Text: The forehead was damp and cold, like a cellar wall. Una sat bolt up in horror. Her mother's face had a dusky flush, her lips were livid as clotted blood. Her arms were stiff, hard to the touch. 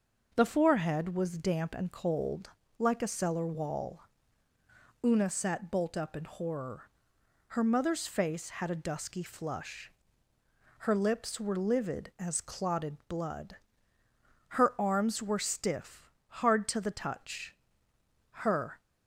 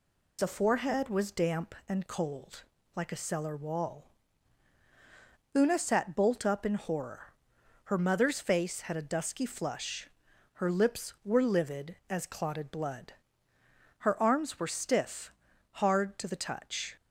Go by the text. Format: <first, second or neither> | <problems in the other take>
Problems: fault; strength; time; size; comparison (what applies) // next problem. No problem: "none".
second | goes on to say "Her"; from 18.2 s on; 0.50 s long